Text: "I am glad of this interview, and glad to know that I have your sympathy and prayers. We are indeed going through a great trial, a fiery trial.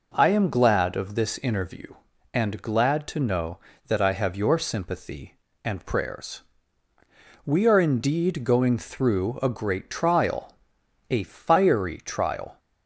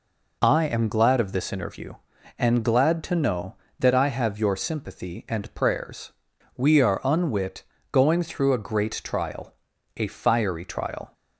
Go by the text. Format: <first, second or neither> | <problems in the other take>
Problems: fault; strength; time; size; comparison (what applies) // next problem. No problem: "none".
first | says "unwit" for "indeed"; at 7.0 s